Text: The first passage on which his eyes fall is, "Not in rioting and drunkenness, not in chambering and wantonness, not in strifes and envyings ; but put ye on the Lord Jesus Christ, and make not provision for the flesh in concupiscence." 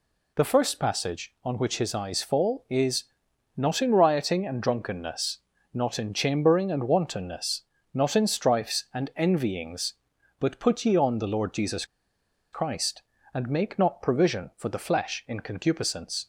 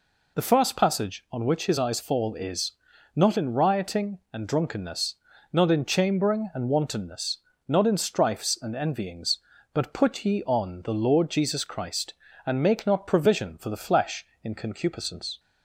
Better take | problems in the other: second | pauses between "Jesus" and "Christ"; noticeable; at 11.8 s; 0.67 s long

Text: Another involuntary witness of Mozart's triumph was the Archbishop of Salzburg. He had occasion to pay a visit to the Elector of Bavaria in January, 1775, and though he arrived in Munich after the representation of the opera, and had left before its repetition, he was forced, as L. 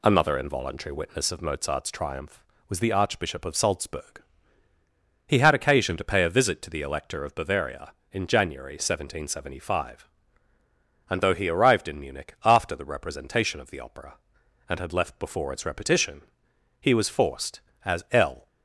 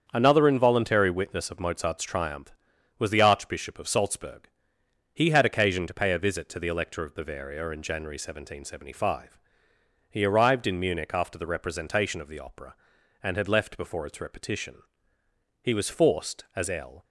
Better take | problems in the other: first | starts louder than the rest; strong; until 1.1 s; 7.5 dB // skips "and though"; at 9.7 s

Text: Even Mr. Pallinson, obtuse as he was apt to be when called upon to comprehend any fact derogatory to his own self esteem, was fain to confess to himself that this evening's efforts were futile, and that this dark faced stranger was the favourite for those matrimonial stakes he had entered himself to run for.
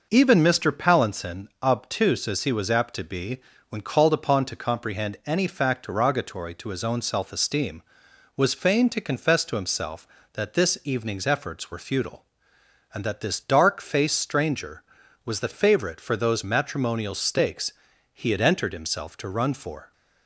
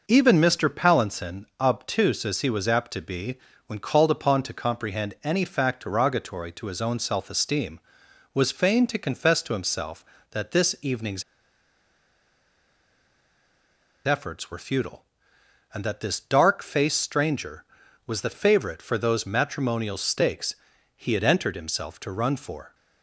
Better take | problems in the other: first | pauses between "be" and "when"; slight; at 3.3 s; 0.30 s long; slight in the first // pauses between "evening's" and "efforts"; strong; at 11.2 s; 2.8 s long // pauses between "stakes" and "he"; at 20.5 s; 0.40 s long; also in the first

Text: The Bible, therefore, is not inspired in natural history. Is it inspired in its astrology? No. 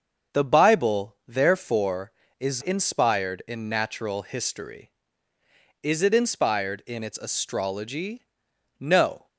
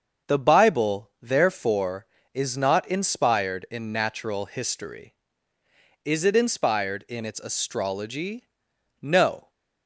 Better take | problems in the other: second | starts louder than the rest; until 1.4 s; 6.5 dB; also in the second // skips "not"; at 2.6 s

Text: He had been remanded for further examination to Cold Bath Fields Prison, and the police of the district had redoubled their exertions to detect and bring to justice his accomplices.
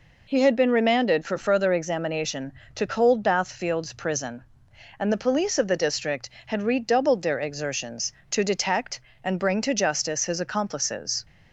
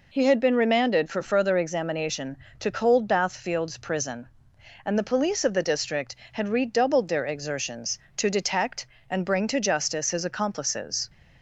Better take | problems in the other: neither | none

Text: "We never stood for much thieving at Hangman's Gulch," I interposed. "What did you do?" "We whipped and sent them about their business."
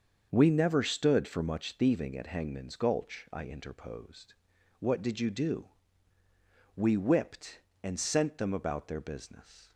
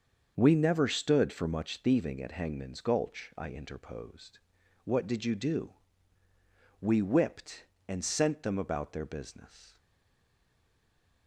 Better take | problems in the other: first | starts louder than the rest; until 1.3 s; 6.5 dB; also in the first // stays silent after the last word; noticeable; from 9.7 s on; 1.5 s long

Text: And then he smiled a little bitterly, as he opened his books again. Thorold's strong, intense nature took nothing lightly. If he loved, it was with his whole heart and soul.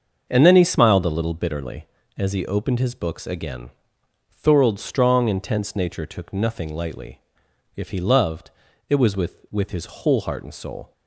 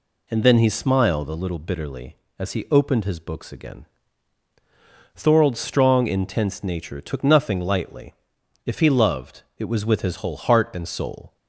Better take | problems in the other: second | starts louder than the rest; until 1.3 s; 6.5 dB // says "with" twice; at 9.4 s

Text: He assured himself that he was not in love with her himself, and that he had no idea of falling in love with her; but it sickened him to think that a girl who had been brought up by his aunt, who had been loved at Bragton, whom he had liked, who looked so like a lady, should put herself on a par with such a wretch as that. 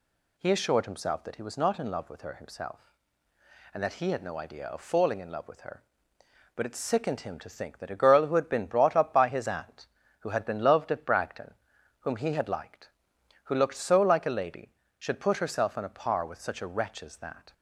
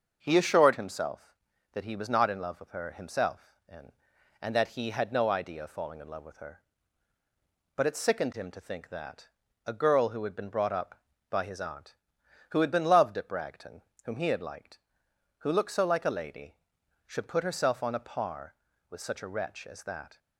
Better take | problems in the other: first | starts louder than the rest; until 1.2 s; 6.5 dB // says "and" twice; at 4.3 s // pauses between "that" and "a"; at 9.2 s; 0.40 s long

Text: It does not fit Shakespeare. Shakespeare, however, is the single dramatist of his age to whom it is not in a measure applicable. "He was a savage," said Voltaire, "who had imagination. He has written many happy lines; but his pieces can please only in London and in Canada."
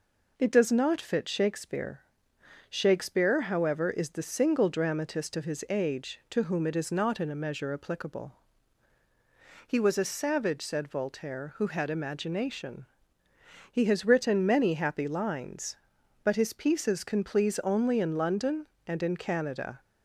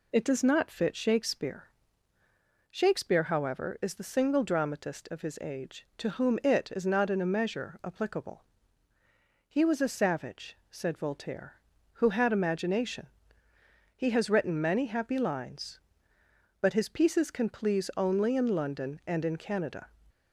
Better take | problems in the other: neither | none

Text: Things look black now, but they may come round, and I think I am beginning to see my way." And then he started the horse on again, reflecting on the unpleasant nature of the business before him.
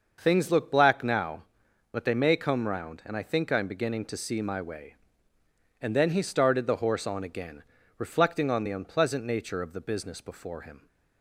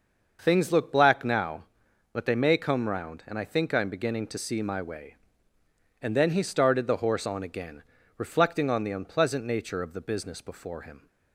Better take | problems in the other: neither | starts louder than the rest; the same in both

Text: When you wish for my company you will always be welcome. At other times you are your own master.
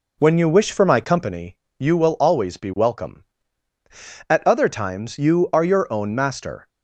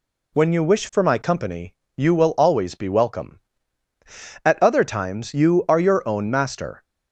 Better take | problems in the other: second | starts louder than the rest; until 1.4 s; 3.5 dB // pauses between "company" and "you"; slight; at 1.5 s; 0.22 s long; slight in the second

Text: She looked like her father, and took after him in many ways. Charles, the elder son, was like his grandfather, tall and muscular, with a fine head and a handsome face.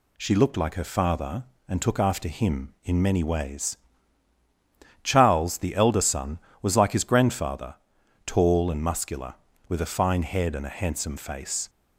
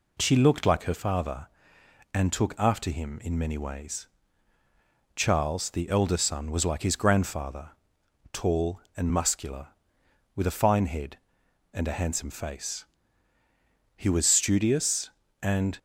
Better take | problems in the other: first | goes on to say "He was studious and"; strong; from 13.9 s on; 1.8 s long

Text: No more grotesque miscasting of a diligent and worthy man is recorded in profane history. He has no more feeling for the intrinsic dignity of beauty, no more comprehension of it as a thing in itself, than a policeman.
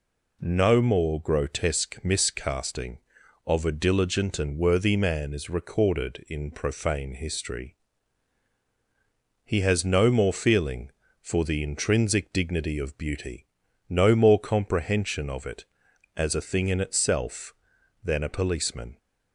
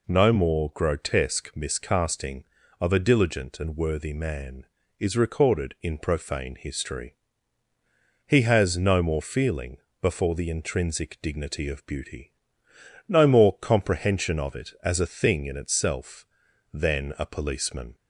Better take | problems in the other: first | says "before" for "for"; at 10.0 s

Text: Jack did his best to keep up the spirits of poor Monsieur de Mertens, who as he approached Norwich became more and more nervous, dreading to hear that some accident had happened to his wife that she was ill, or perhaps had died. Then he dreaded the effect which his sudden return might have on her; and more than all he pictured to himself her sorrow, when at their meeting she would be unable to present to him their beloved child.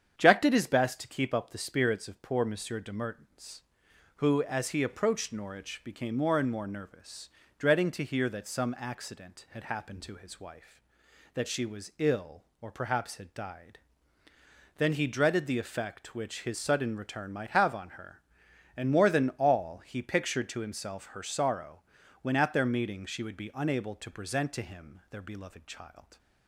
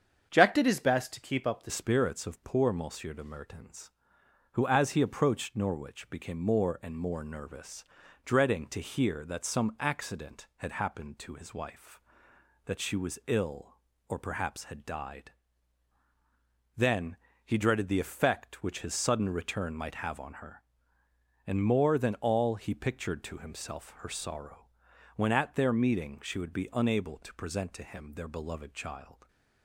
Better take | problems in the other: first | starts louder than the rest; strong; until 1.3 s; 7.5 dB; strong in the first // changes voice at "spirits"; from 1.6 s on; 27.6 s long // pauses between "Then" and "he"; slight; at 17.1 s; 0.30 s long

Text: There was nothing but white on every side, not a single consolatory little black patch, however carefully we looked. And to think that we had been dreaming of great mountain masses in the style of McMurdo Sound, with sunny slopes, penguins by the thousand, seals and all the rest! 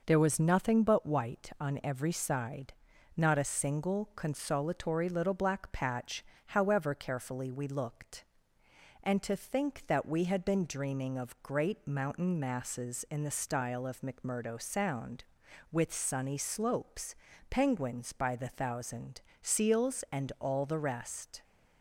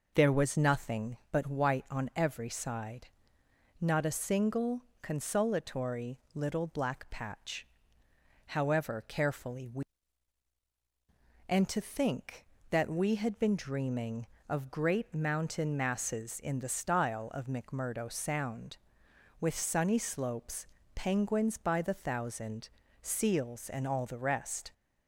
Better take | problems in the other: first | pauses between "single" and "consolatory"; slight; at 4.8 s; 0.20 s long // pauses between "consolatory" and "little"; slight; at 6.1 s; 0.16 s long // skips "looked"; at 10.6 s

